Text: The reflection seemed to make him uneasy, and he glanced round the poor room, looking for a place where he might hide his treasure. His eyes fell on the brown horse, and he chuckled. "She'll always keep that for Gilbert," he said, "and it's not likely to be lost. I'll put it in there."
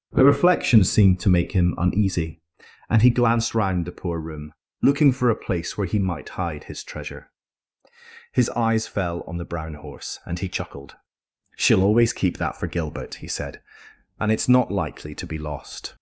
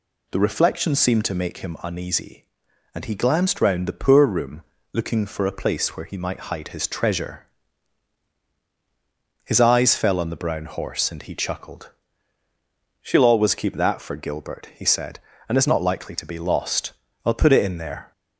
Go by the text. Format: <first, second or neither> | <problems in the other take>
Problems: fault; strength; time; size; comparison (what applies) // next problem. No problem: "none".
second | starts louder than the rest; until 1.1 s; 6.5 dB // stops before "I'll put it in there"; at 15.9 s